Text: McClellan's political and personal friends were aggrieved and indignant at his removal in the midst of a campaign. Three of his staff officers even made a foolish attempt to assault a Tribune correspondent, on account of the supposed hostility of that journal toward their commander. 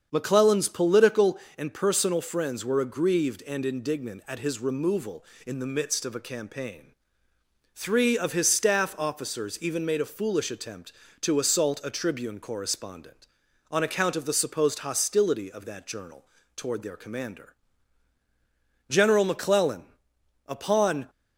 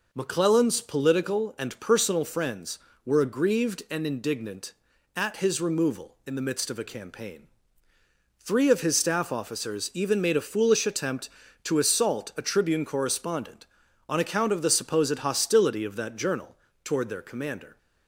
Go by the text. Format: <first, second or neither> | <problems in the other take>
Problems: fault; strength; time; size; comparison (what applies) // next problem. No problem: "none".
second | starts louder than the rest; strong; until 1.1 s; 7 dB // pauses between "journal" and "toward"; slight; at 16.2 s; 0.32 s long; slight in the second // goes on to say "General McClellan upon"; strong; from 18.8 s on; 2.2 s long